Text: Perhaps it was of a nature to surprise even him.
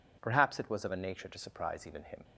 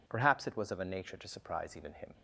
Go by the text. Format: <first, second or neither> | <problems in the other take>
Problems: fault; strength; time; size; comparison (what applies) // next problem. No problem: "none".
neither | none